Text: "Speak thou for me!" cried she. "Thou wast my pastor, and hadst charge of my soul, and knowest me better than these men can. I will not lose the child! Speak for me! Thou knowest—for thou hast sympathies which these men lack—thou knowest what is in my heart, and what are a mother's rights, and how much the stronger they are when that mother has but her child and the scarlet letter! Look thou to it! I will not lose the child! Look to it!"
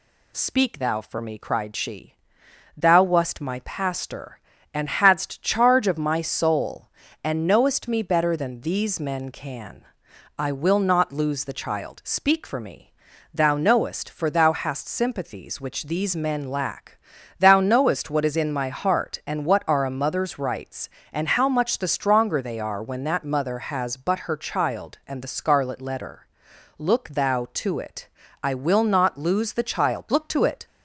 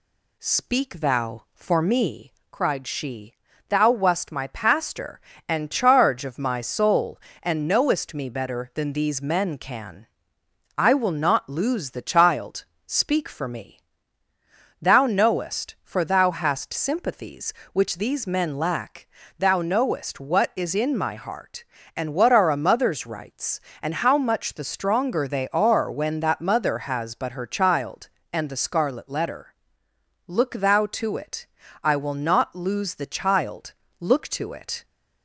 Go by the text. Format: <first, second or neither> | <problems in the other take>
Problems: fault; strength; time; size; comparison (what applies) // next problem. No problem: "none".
first | skips "hadst"; at 5.7 s